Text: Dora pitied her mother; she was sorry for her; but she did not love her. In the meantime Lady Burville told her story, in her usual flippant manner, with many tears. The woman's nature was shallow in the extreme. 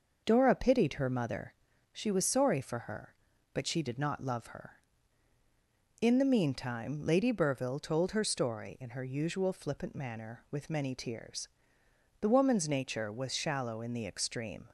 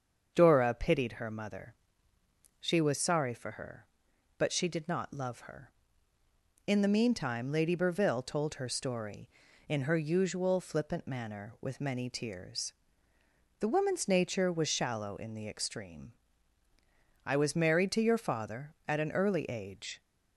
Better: first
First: none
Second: starts louder than the rest; until 1.3 s; 7 dB // goes on to say "I was married to your father at an early age"; strong; from 17.2 s on; 2.7 s long

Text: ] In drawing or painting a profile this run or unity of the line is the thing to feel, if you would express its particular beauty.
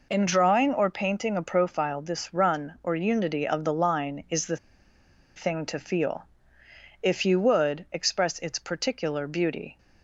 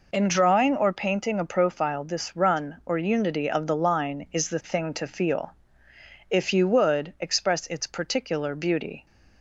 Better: second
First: pauses between "the" and "thing"; noticeable; at 4.5 s; 0.79 s long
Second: none

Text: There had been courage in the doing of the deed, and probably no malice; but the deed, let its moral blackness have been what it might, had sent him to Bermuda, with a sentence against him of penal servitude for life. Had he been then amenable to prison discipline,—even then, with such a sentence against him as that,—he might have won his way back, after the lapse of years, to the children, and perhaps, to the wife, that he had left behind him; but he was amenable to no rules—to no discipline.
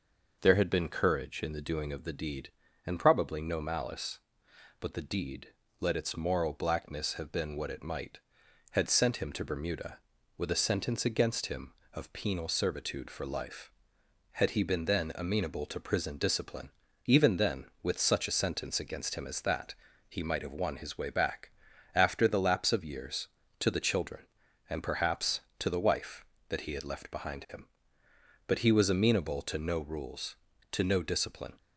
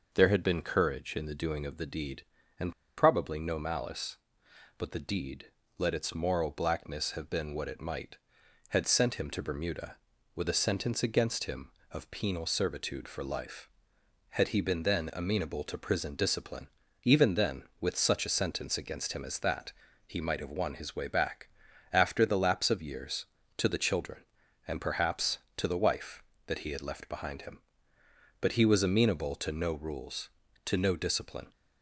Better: first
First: none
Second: pauses between "and" and "probably"; slight; at 2.7 s; 0.25 s long

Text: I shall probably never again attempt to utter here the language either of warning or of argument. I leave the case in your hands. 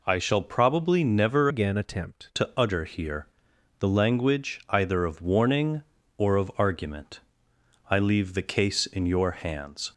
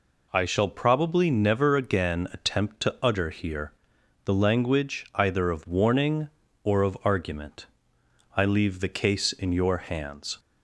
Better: second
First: changes voice from "again" to "attempt"; from 1.5 to 2.3 s; 0.8 s long // pauses between "here" and "the"; noticeable; at 3.2 s; 0.54 s long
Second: pauses between "here" and "the"; noticeable; at 3.7 s; 0.54 s long

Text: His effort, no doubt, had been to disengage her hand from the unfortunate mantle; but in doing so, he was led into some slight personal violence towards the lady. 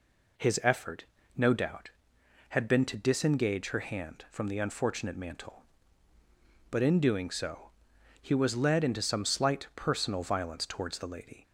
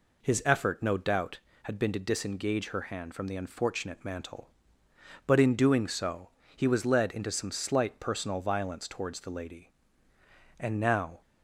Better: first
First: none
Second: goes on to say "And now"; noticeable; from 10.5 s on; 0.62 s long

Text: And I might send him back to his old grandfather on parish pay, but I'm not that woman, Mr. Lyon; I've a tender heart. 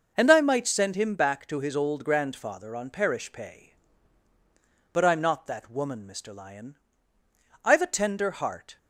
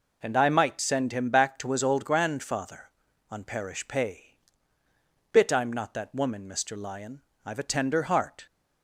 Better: first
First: none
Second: says "bit" for "but"; at 5.3 s

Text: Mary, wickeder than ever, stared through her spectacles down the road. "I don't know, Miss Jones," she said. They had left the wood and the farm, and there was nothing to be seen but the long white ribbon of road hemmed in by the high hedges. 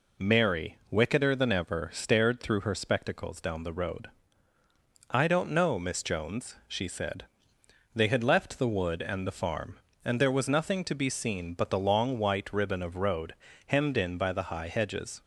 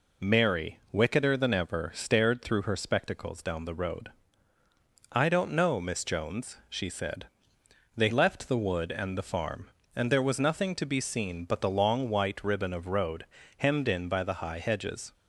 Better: first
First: pauses between "road" and "hemmed"; slight; at 13.3 s; 0.34 s long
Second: skips "had"; at 8.1 s // pauses between "road" and "hemmed"; slight; at 13.2 s; 0.34 s long

